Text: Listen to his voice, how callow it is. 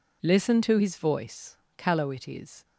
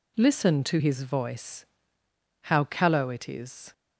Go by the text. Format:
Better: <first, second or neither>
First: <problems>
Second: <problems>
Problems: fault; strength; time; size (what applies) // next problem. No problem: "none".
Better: second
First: skips "how"; at 1.6 s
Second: none